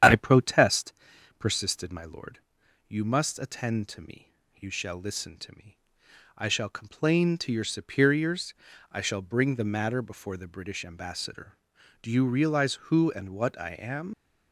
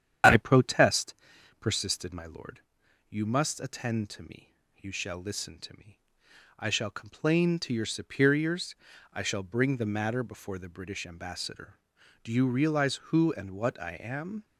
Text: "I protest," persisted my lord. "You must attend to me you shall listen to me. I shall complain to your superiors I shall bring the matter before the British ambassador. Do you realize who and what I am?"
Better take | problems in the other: second | starts louder than the rest; strong; until 1.5 s; 9.5 dB; strong in the second // pauses between "me" and "you"; slight; at 4.3 s; 0.20 s long; slight in the second // pauses between "superiors" and "I"; at 8.5 s; 0.40 s long; also in the second // leaves "am" unfinished; at 14.1 s; 100 ms

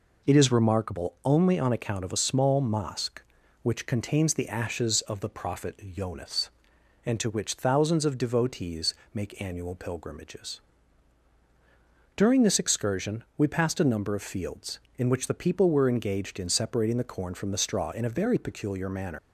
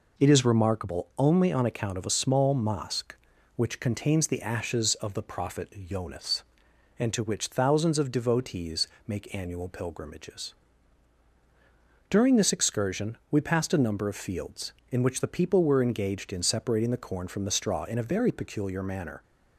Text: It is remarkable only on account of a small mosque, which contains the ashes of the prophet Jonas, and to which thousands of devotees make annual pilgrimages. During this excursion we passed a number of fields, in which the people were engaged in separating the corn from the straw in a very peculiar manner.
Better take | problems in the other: second | pauses between "devotees" and "make"; slight; at 8.9 s; 0.18 s long; slight in the second // leaves "manner" unfinished; at 19.1 s; 100 ms

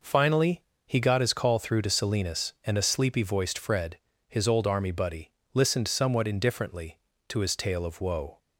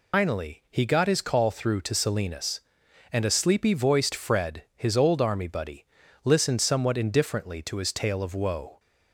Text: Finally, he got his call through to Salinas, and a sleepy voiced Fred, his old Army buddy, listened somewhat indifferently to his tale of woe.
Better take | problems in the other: first | loses the start of "Finally"; at 0.1 s; 200 ms

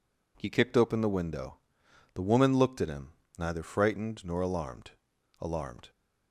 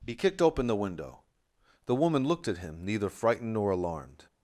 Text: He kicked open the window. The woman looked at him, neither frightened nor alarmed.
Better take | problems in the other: second | says "alarmed" twice; at 5.4 s

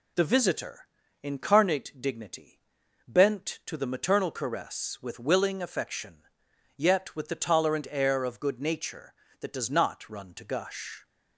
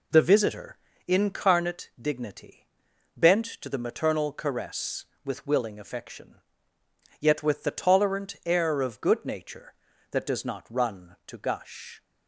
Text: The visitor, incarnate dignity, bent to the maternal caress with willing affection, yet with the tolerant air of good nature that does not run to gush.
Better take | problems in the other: neither | none

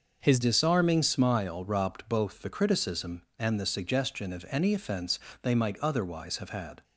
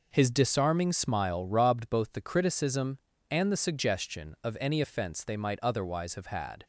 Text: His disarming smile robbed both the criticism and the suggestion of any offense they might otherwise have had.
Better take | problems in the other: second | starts louder than the rest; noticeable; until 1.2 s; 6 dB // changes voice at "disarming"; from 0.3 s on; 6.5 s long // pauses between "offense" and "they"; slight; at 5.1 s; 0.24 s long

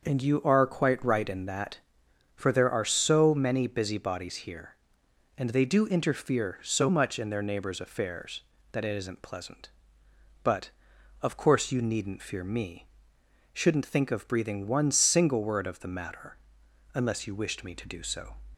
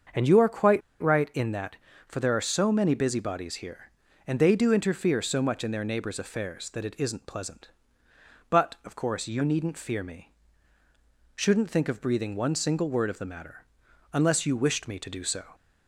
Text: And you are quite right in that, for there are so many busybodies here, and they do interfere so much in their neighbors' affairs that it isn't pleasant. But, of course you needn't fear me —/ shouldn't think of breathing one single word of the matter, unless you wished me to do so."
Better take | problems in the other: first | starts louder than the rest; until 1.4 s; 6.5 dB; also in the first // pauses between "quite" and "right"; slight; at 0.8 s; 0.19 s long

